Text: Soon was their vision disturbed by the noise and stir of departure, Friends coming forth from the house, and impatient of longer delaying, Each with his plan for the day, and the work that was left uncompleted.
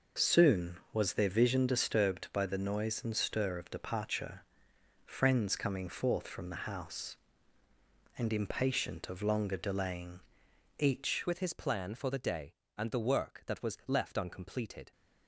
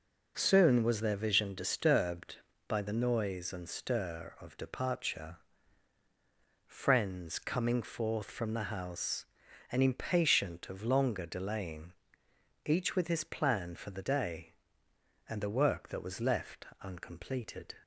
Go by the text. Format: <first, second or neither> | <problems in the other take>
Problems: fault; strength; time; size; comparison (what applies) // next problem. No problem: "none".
second | changes voice at "with"; from 11.2 s on; 3.7 s long